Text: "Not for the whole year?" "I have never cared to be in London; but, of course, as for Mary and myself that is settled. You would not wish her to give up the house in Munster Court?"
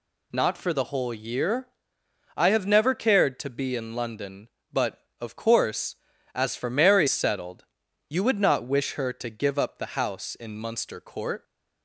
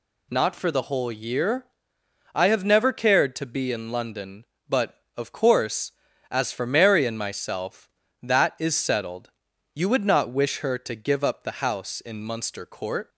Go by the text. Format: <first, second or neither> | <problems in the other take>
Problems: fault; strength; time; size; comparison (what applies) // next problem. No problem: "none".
second | skips "and myself that is"; at 7.0 s